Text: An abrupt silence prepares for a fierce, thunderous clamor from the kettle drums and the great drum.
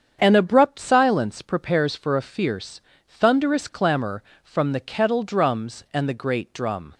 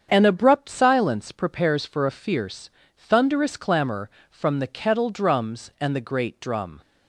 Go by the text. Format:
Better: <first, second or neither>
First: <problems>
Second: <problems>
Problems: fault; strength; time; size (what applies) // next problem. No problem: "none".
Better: neither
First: starts louder than the rest; strong; until 1.2 s; 7.5 dB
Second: starts louder than the rest; strong; until 1.1 s; 7.5 dB